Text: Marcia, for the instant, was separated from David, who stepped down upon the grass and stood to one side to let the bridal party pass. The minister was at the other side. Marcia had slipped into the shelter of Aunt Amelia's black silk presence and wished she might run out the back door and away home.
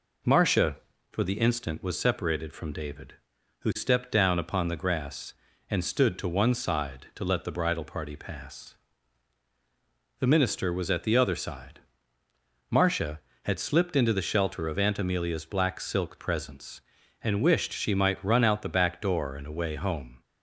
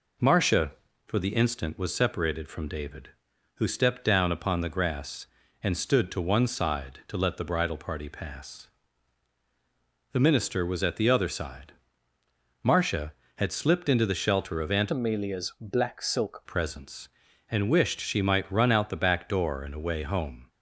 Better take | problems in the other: first | changes voice from "Amelia's" to "silk"; from 14.9 to 16.4 s; 1.5 s long

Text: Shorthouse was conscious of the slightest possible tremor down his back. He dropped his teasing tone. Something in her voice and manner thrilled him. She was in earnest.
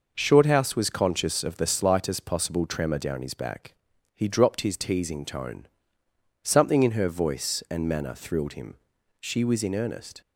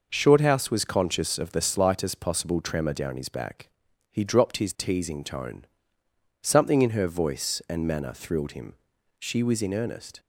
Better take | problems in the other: neither | none

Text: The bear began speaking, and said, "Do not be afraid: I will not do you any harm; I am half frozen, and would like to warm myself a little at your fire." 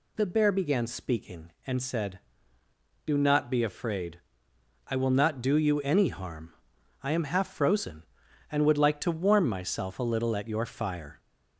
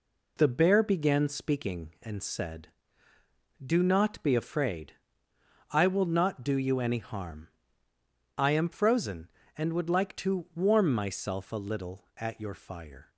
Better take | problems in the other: first | skips "half"; at 8.6 s

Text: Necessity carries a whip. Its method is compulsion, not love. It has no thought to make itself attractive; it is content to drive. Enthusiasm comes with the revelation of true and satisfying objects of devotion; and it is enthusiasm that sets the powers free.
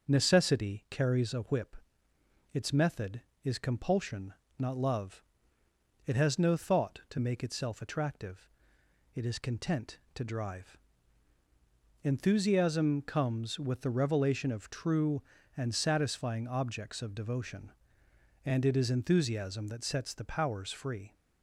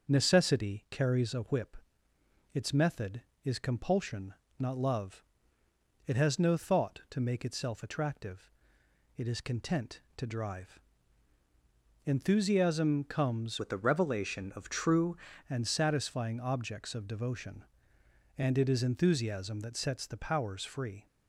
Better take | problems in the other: first | starts louder than the rest; until 1.1 s; 6.5 dB; also in the first // changes voice from "with" to "true"; from 13.5 to 15.1 s; 1.6 s long

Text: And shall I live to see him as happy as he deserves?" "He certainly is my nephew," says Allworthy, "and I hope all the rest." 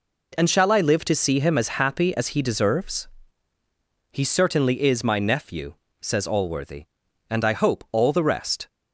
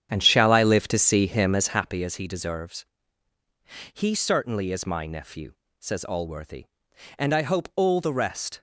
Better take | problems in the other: first | starts louder than the rest; strong; until 2.0 s; 9 dB

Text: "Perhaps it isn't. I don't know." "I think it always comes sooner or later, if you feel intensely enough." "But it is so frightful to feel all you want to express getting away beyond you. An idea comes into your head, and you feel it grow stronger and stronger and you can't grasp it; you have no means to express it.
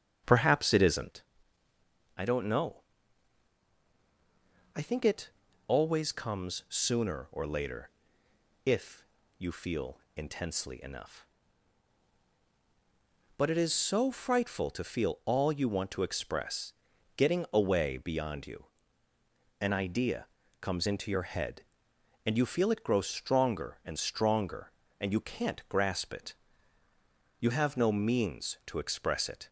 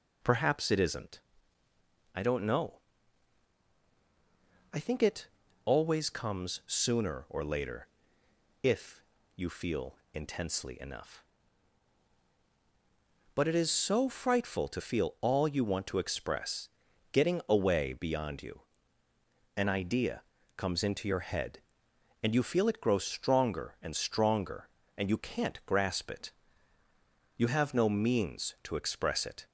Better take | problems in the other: second | starts louder than the rest; strong; until 1.2 s; 8 dB // pauses between "it" and "always"; at 5.2 s; 0.38 s long; also in the second // pauses between "if" and "you"; slight; at 9.0 s; 0.32 s long; slight in the second // pauses between "feel" and "intensely"; slight; at 9.9 s; 0.16 s long; slight in the second // pauses between "express" and "getting"; noticeable; at 16.7 s; 0.46 s long; noticeable in the second // pauses between "idea" and "comes"; slight; at 20.2 s; 0.36 s long; slight in the second

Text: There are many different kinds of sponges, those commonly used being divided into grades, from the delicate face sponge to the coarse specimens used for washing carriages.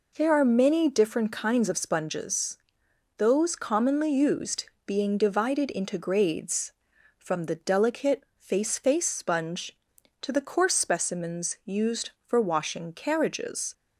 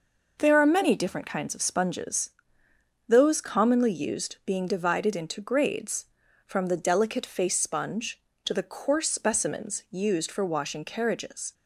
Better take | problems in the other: second | pauses between "used" and "being"; slight; at 4.6 s; 0.20 s long // says "face" twice; at 8.7 s

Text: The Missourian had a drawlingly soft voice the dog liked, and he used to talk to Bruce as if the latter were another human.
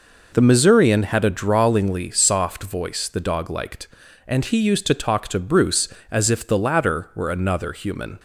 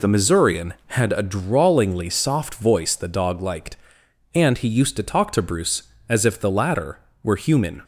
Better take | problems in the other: first | skips "another"; at 7.3 s

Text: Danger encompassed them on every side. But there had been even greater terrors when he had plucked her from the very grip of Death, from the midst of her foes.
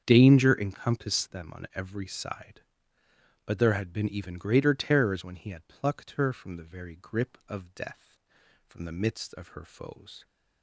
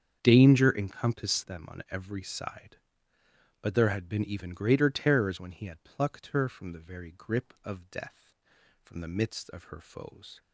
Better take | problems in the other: neither | starts louder than the rest; strong; the same in both

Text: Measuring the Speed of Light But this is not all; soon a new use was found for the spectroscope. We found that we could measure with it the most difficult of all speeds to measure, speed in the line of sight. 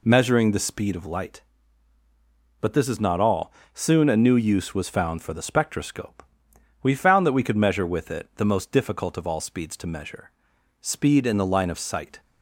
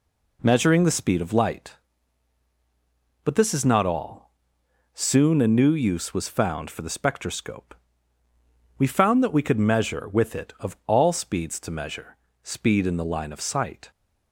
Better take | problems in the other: first | skips "the most difficult"; at 10.5 s

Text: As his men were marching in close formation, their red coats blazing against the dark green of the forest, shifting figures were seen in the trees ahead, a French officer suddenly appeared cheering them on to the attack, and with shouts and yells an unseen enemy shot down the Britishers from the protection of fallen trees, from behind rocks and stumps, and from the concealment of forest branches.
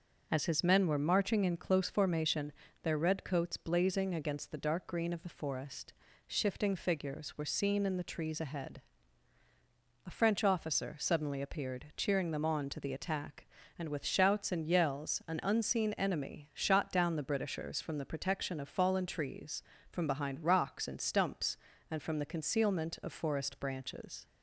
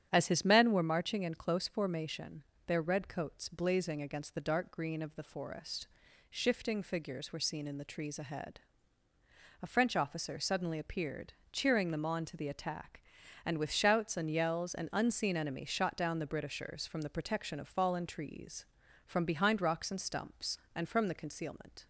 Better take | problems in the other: first | starts louder than the rest; strong; until 1.1 s; 9.5 dB // pauses between "appeared" and "cheering"; slight; at 11.3 s; 0.18 s long // stops before "of forest branches"; at 21.8 s

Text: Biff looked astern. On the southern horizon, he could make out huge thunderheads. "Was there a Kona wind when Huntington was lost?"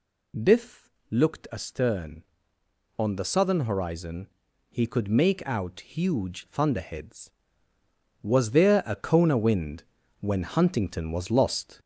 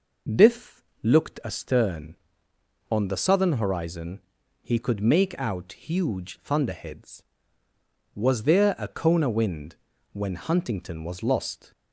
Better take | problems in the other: second | gets louder; noticeable; throughout; 5 dB // pauses between "Biff" and "looked"; slight; at 0.8 s; 0.20 s long; slight in the second // pauses between "wind" and "when"; slight; at 9.8 s; 0.36 s long; slight in the second

